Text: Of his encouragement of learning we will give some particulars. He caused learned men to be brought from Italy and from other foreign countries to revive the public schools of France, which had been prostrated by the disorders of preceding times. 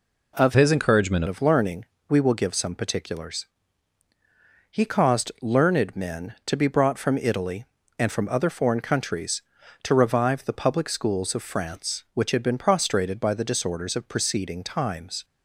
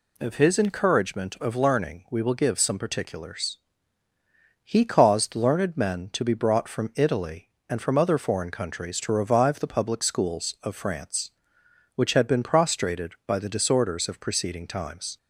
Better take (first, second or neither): second